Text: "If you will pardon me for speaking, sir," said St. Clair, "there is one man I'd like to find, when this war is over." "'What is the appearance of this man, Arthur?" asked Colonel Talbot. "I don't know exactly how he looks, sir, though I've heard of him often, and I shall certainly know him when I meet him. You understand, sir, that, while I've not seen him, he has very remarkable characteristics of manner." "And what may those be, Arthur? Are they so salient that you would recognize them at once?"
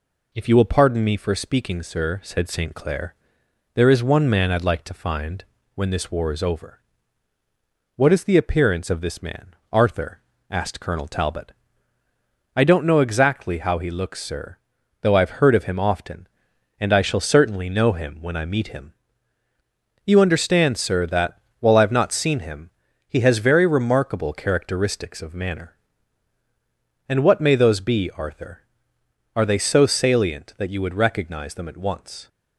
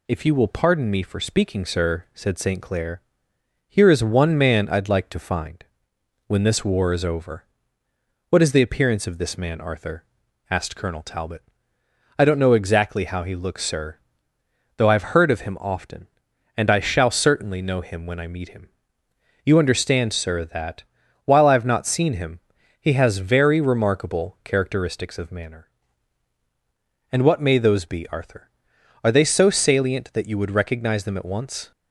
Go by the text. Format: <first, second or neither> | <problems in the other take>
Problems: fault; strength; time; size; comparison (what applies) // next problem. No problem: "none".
first | says "here" for "there"; at 3.6 s